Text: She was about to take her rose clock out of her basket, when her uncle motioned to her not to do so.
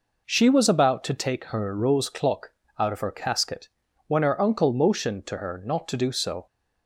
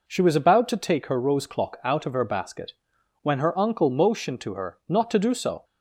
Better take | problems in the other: second | pauses between "clock" and "out"; slight; at 2.5 s; 0.26 s long // says "casket" for "basket"; at 3.1 s

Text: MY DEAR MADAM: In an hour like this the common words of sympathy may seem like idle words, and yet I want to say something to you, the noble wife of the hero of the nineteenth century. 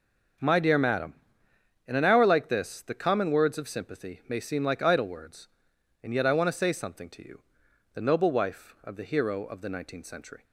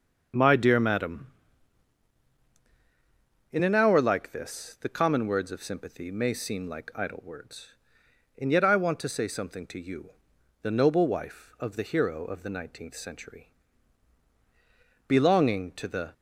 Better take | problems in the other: first | starts louder than the rest; noticeable; until 3.6 s; 6 dB; noticeable in the first // goes on to say "Belonging to the"; noticeable; from 15.0 s on; 1.0 s long

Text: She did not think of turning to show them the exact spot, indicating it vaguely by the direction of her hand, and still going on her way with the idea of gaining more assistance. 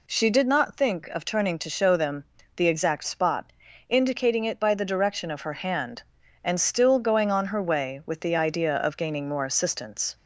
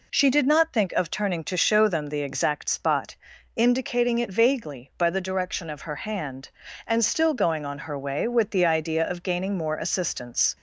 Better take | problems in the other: second | pauses between "them" and "the"; slight; at 2.2 s; 0.32 s long // skips "vaguely"; at 4.5 s

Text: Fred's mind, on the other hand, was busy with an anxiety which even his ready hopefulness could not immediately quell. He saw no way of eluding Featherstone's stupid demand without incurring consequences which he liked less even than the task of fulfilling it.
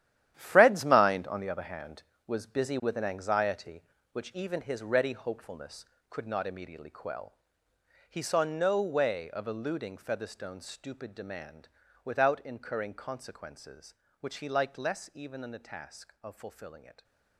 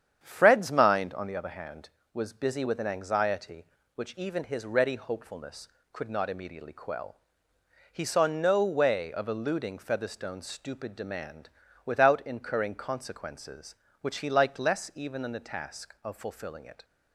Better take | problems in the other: second | gets quieter; strong; throughout; 11.5 dB // starts louder than the rest; strong; until 1.3 s; 11.5 dB; strong in the second // pauses between "demand" and "without"; slight; at 11.6 s; 0.36 s long; slight in the second

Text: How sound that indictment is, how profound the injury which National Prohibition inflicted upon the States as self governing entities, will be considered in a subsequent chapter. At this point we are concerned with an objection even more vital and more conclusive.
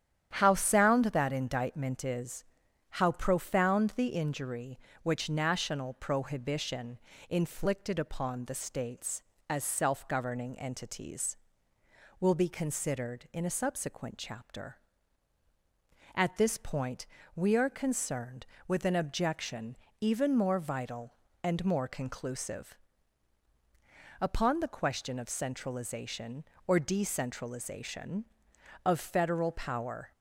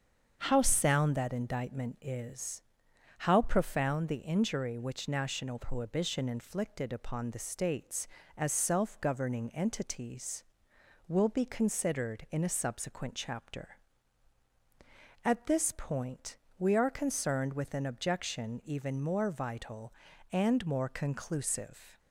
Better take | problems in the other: second | starts louder than the rest; strong; until 1.3 s; 10 dB; also in the second // pauses between "Prohibition" and "inflicted"; slight; at 6.9 s; 0.30 s long // pauses between "point" and "we"; slight; at 17.0 s; 0.30 s long; slight in the second // pauses between "objection" and "even"; slight; at 19.7 s; 0.24 s long // goes on to say "Upon the question of centralization or decentralization of Federal power"; strong; from 24.2 s on; 5.9 s long

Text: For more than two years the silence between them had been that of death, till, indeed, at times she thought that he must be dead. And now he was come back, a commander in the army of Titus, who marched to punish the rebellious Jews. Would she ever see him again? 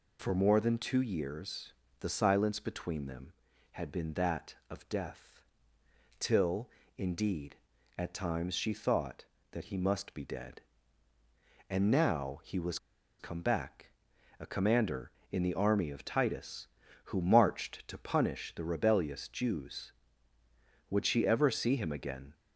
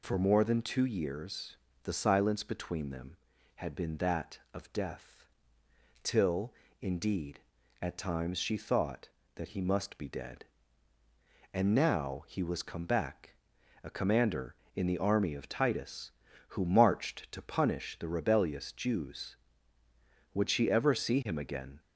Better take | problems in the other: second | pauses between "years" and "the"; slight; at 1.7 s; 0.28 s long; slight in the second // pauses between "was" and "come"; at 12.7 s; 0.42 s long

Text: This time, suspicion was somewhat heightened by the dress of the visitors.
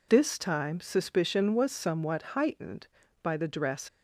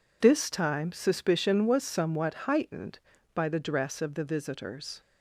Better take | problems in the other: second | stops before "of the visitors"; at 3.8 s

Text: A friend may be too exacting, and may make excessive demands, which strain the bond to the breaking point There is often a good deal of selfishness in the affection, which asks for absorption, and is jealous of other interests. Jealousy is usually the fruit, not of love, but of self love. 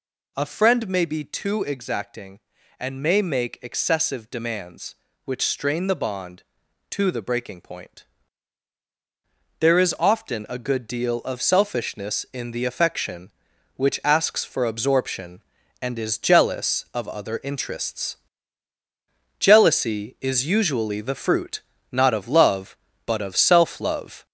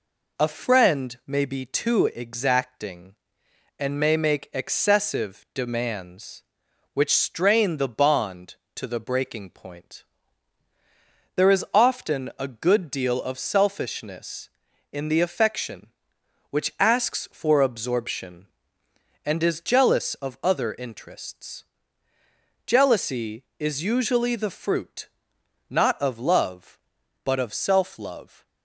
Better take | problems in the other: second | gets louder; noticeable; throughout; 5 dB // pauses between "point" and "There"; strong; at 8.0 s; 1.5 s long; strong in the second

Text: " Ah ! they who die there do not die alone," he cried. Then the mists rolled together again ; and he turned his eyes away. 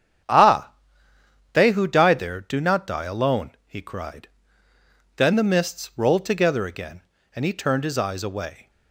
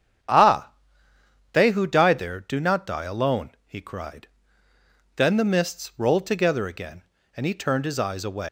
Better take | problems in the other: first | starts louder than the rest; strong; until 2.0 s; 8.5 dB; strong in the first // leaves "away" unfinished; at 8.4 s; 215 ms

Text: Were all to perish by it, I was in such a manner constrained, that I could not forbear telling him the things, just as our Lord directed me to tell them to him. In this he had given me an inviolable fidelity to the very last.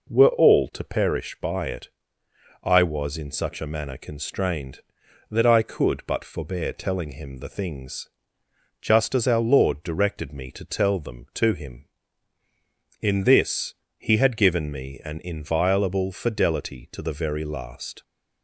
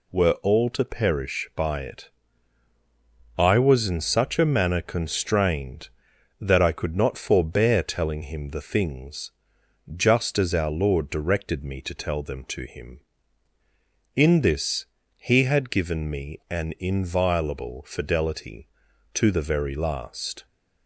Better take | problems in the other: second | says "but" for "not"; at 6.0 s // pauses between "this" and "he"; slight; at 13.7 s; 0.24 s long; slight in the second

